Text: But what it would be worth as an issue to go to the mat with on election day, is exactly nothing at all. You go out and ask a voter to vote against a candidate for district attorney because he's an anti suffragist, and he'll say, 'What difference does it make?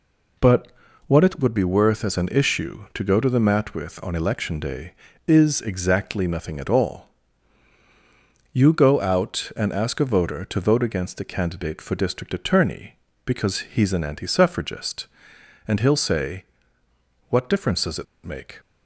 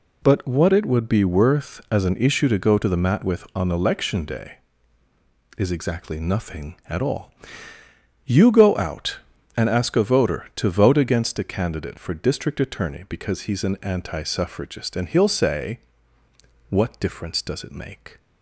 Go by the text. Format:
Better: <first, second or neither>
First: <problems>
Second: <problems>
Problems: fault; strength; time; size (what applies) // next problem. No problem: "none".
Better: second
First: pauses between "But" and "what"; at 0.6 s; 0.38 s long // pauses between "it" and "make"; slight; at 18.0 s; 0.20 s long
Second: none